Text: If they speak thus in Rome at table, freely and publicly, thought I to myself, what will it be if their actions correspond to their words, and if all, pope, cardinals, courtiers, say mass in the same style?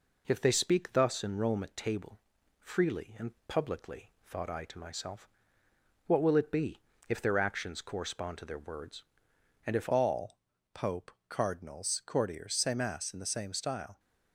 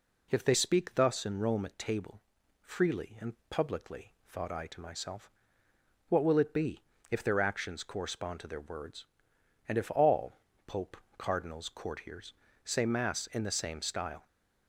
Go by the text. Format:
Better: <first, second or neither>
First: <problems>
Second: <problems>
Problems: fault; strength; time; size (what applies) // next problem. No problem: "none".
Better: second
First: pauses between "and" and "publicly"; slight; at 3.3 s; 0.16 s long // pauses between "be" and "if"; slight; at 6.7 s; 0.30 s long // changes voice at "all"; from 9.9 s on; 4.0 s long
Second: pauses between "and" and "publicly"; slight; at 3.3 s; 0.16 s long // pauses between "be" and "if"; slight; at 6.8 s; 0.30 s long